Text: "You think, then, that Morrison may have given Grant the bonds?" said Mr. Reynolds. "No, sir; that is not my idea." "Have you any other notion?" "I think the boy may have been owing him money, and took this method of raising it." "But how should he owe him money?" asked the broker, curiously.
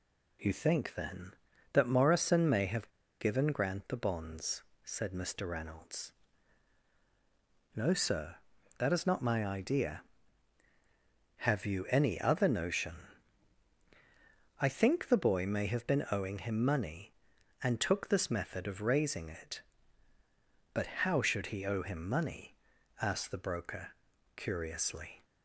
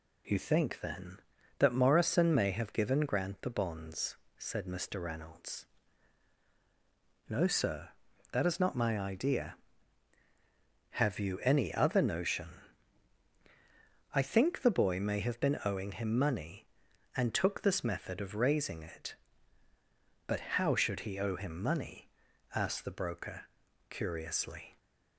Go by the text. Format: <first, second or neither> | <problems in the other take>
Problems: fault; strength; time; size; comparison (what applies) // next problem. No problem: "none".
second | pauses between "have" and "given"; slight; at 2.8 s; 0.32 s long // pauses between "But" and "how"; slight; at 20.8 s; 0.16 s long; slight in the second